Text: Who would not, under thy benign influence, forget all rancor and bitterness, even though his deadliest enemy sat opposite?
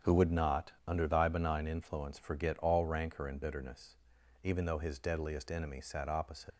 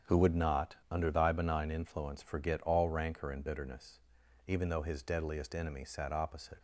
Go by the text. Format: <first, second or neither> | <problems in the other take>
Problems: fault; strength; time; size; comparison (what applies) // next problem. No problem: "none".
second | starts louder than the rest; strong; until 1.2 s; 8 dB; strong in the second // leaves "opposite" unfinished; at 6.5 s; 50 ms